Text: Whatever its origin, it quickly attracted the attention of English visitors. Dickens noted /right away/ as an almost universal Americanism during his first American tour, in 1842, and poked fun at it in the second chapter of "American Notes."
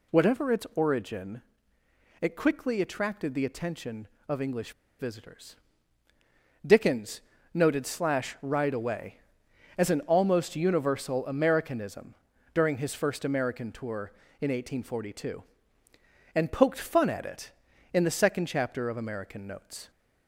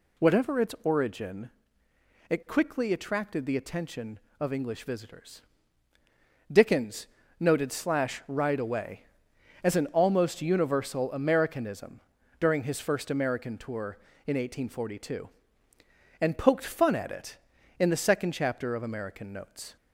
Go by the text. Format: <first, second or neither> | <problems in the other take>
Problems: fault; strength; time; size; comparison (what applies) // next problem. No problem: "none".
second | pauses between "English" and "visitors"; slight; at 4.7 s; 0.26 s long // pauses between "Dickens" and "noted"; slight; at 7.2 s; 0.32 s long; slight in the second // pauses between "Americanism" and "during"; slight; at 12.1 s; 0.36 s long; slight in the second